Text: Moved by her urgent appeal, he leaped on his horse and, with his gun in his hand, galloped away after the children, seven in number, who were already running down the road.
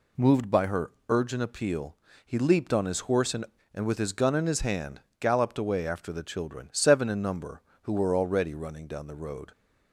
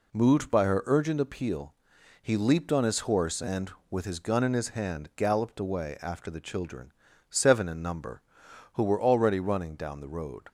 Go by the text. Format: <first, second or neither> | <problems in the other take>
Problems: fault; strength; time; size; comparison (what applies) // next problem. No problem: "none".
second | pauses between "her" and "urgent"; slight; at 0.9 s; 0.18 s long // says "and" twice; at 3.7 s